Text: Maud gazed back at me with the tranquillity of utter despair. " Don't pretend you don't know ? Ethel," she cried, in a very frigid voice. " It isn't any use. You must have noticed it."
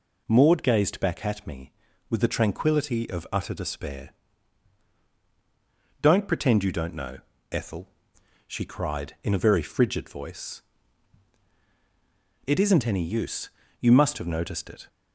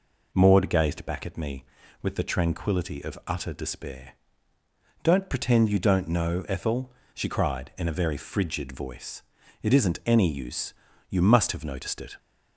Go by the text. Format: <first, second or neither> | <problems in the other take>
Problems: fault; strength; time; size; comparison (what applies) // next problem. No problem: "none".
neither | none